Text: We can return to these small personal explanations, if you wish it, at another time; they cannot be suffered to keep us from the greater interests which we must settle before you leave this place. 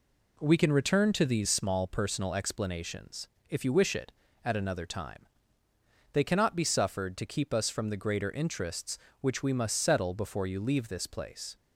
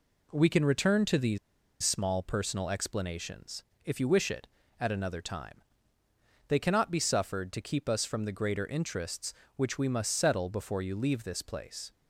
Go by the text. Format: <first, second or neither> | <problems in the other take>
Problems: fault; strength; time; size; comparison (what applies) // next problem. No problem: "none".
first | pauses between "these" and "small"; at 1.3 s; 0.44 s long